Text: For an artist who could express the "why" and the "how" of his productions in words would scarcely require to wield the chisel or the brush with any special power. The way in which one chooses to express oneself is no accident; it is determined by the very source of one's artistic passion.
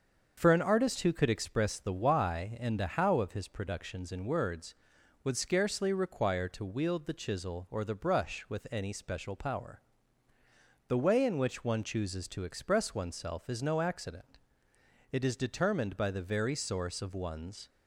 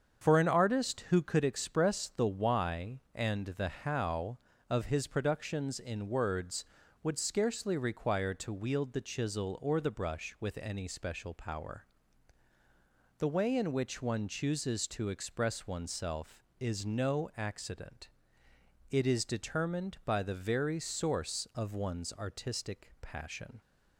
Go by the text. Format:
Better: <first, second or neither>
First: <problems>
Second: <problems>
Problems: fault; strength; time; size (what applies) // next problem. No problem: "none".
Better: second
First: starts louder than the rest; until 1.3 s; 6.5 dB // stops before "artistic passion"; at 17.6 s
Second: starts louder than the rest; strong; until 1.3 s; 7 dB